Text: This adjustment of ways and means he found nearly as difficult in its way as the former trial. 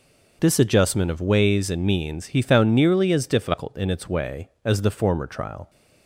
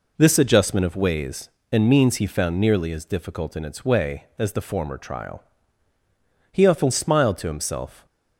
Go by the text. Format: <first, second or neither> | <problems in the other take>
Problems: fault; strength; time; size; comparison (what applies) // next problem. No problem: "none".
first | goes on to say "He often smiled to himself"; from 6.5 s on; 1.5 s long